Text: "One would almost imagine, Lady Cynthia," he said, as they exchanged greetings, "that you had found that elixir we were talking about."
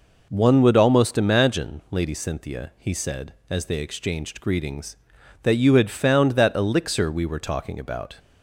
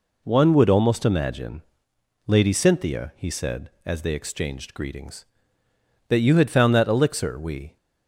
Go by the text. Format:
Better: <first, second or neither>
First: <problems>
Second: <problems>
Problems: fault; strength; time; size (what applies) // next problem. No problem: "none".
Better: first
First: none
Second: stops before "were talking about"; at 7.7 s